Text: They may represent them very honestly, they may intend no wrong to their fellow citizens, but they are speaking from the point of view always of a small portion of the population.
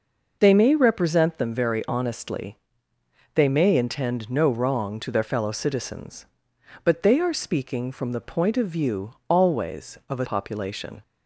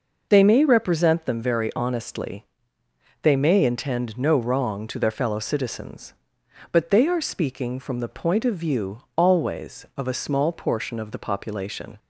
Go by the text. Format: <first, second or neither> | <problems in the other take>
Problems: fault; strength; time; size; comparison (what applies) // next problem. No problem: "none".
second | skips "small portion of the"; at 10.2 s